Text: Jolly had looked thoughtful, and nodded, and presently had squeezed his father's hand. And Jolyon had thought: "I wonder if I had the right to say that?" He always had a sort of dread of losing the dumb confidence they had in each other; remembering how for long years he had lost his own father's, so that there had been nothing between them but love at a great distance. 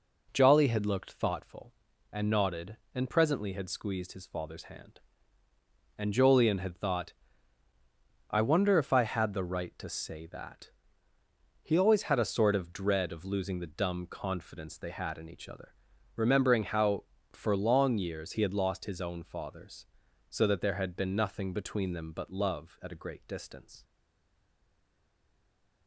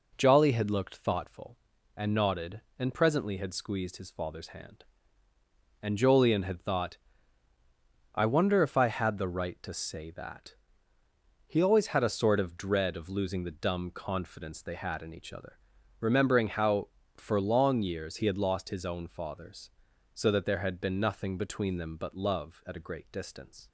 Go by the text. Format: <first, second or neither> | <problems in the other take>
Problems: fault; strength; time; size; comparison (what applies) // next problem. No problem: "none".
second | stays silent after the last word; noticeable; from 23.8 s on; 2.0 s long